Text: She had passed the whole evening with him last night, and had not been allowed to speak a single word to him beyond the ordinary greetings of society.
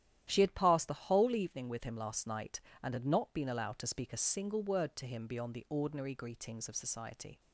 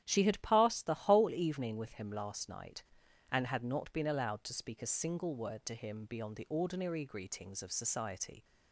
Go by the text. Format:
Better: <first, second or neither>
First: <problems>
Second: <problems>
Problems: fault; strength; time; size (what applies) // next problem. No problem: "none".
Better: neither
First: starts louder than the rest; strong; until 1.2 s; 11.5 dB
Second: starts louder than the rest; strong; until 1.0 s; 10.5 dB